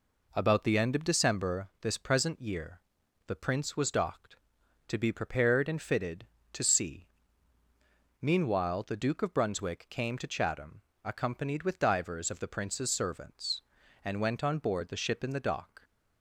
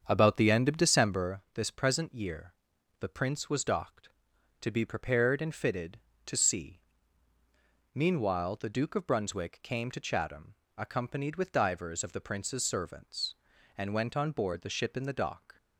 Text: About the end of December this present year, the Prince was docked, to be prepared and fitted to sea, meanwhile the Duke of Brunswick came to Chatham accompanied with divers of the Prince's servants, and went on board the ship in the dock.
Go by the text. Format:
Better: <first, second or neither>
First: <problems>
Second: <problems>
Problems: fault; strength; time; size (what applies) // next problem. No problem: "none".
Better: first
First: pauses between "Chatham" and "accompanied"; slight; at 10.8 s; 0.22 s long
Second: starts louder than the rest; strong; until 1.3 s; 7.5 dB // pauses between "Chatham" and "accompanied"; slight; at 10.5 s; 0.22 s long